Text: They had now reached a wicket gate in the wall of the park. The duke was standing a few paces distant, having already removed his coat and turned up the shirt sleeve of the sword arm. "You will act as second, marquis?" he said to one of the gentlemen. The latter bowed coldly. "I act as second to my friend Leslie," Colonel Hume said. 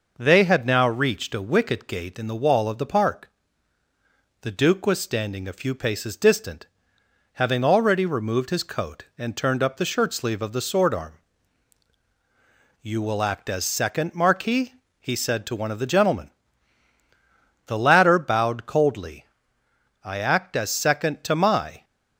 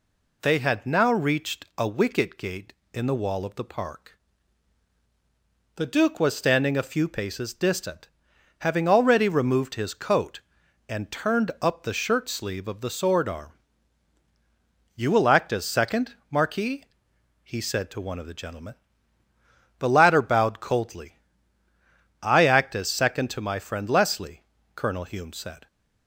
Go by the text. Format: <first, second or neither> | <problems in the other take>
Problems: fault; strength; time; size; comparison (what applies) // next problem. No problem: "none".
second | stops before "friend Leslie Colonel Hume said"; at 21.8 s